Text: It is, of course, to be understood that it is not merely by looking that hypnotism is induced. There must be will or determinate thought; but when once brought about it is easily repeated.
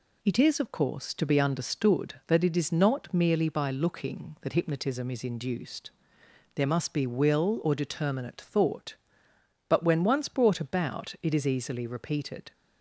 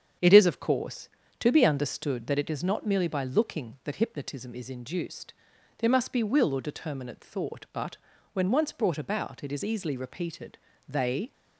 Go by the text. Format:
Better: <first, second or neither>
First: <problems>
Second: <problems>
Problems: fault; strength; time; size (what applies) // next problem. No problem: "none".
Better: first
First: none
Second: starts louder than the rest; strong; until 1.5 s; 8 dB // pauses between "but" and "when"; slight; at 7.9 s; 0.36 s long // goes on to say "They"; slight; from 10.8 s on; 0.44 s long